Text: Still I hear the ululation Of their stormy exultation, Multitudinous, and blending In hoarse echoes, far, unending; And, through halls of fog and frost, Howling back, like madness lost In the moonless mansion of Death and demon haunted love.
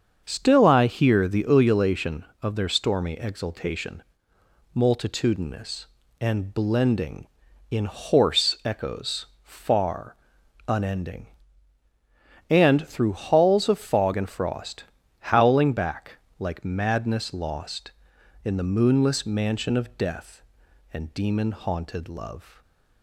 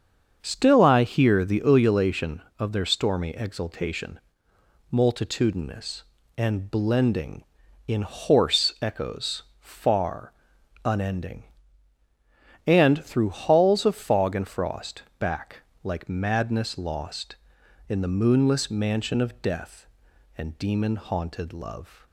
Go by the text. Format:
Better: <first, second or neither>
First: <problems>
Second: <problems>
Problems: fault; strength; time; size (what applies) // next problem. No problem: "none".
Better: first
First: starts louder than the rest; until 1.2 s; 7 dB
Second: starts louder than the rest; until 1.4 s; 7 dB // skips "Howling"; at 15.1 s